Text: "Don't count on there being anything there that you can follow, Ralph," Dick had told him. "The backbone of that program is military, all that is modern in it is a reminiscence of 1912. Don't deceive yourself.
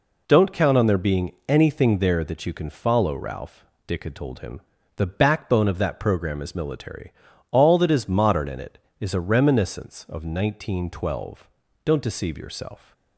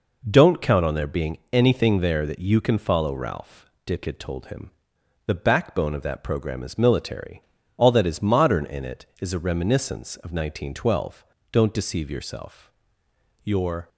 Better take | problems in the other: first | goes on to say "Your"; slight; from 13.4 s on; 0.46 s long

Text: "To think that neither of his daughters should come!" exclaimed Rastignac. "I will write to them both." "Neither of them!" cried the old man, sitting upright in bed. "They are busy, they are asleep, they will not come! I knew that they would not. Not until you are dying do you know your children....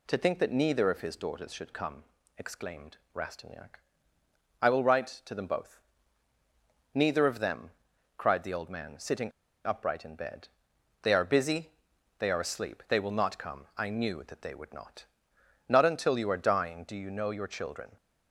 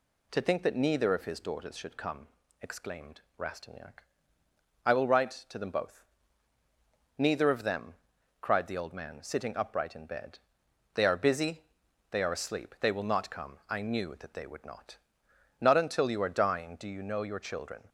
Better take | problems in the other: second | pauses between "exclaimed" and "Rastignac"; slight; at 2.9 s; 0.18 s long; slight in the second // pauses between "sitting" and "upright"; slight; at 9.3 s; 0.33 s long

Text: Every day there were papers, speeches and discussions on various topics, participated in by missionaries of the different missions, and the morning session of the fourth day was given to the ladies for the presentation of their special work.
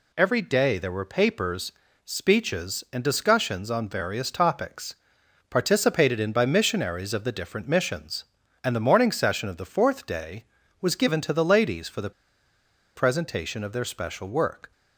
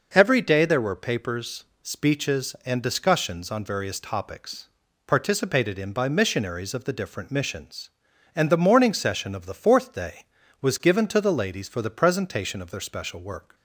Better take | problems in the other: second | pauses between "the" and "presentation"; noticeable; at 12.1 s; 0.85 s long

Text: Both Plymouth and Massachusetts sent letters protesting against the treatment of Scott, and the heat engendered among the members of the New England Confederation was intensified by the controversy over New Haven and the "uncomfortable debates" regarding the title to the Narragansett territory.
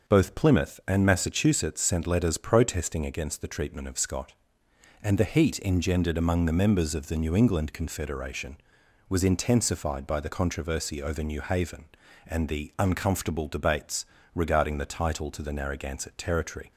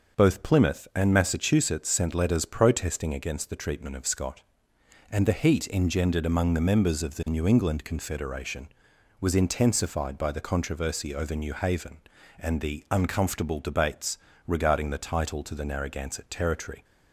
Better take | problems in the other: neither | starts louder than the rest; the same in both // pauses between "debates" and "regarding"; slight; the same in both

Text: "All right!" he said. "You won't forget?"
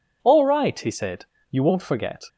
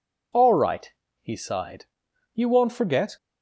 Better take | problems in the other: first | says "sighed" for "said"; at 1.3 s

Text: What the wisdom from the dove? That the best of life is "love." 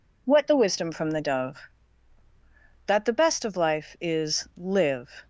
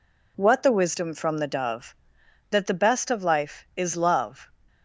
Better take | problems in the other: second | says "live" for "love"; at 4.5 s

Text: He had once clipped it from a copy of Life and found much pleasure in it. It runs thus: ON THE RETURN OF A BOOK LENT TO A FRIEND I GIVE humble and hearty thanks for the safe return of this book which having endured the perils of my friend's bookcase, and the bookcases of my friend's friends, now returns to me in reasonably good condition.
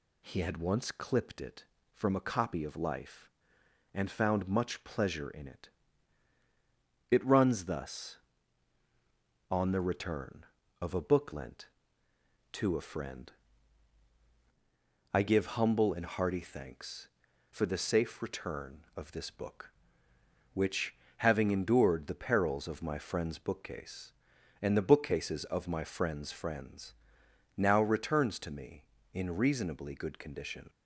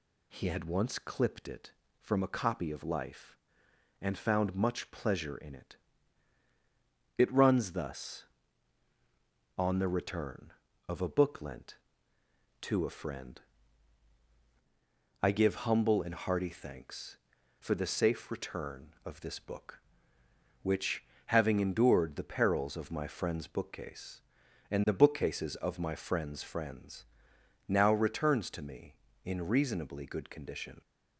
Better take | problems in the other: neither | pauses between "FRIEND" and "I"; strong; the same in both // pauses between "which" and "having"; slight; the same in both

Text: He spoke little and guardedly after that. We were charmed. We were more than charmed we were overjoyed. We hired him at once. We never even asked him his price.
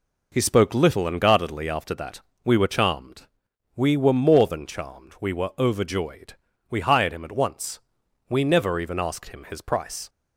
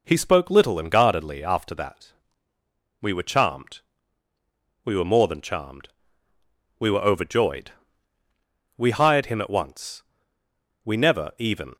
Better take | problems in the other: first | pauses between "charmed" and "we"; noticeable; at 5.8 s; 0.88 s long; slight in the first // stops before "asked him his price"; at 11.7 s

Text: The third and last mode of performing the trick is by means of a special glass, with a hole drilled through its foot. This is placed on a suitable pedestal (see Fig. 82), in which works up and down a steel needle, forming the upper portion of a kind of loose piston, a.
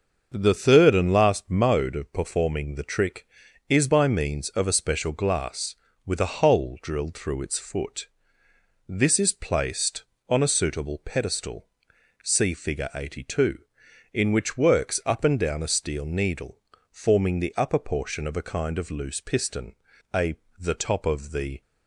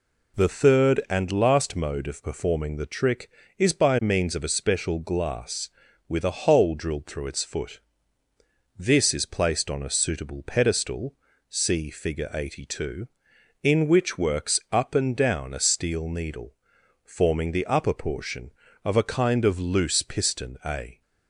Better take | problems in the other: second | starts louder than the rest; until 1.3 s; 6.5 dB // goes on to say "The top of the"; noticeable; from 20.5 s on; 1.0 s long

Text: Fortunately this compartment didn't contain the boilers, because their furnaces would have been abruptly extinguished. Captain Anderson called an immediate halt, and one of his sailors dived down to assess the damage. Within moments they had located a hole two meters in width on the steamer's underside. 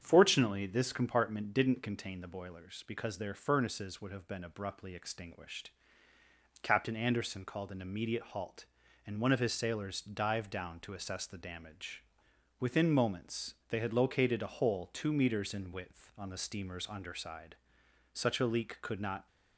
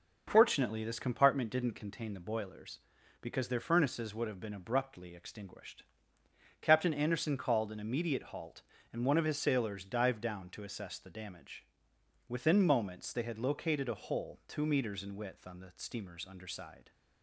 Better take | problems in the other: second | starts louder than the rest; strong; until 1.0 s; 7.5 dB // pauses between "moments" and "they"; slight; at 13.5 s; 0.16 s long // goes on to say "Such a leak could not"; noticeable; from 18.1 s on; 1.1 s long

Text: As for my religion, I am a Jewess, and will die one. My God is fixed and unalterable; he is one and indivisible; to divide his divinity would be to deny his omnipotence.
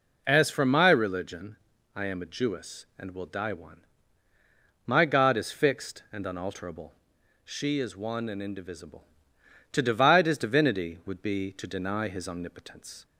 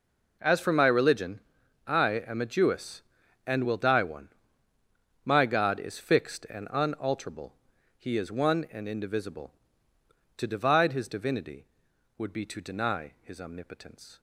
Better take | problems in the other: second | says "she" for "he"; at 7.4 s

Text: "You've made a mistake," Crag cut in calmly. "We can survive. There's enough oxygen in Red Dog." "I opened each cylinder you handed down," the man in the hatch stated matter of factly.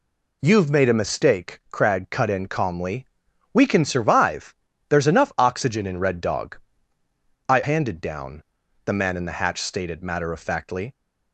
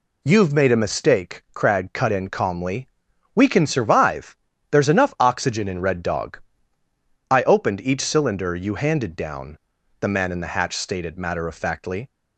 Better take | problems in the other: second | skips "opened each cylinder you"; at 7.6 s

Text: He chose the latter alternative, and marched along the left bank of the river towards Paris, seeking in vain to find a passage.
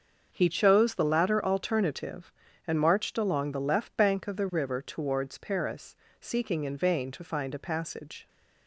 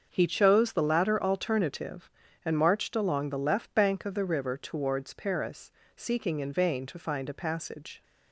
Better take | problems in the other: neither | starts louder than the rest; the same in both

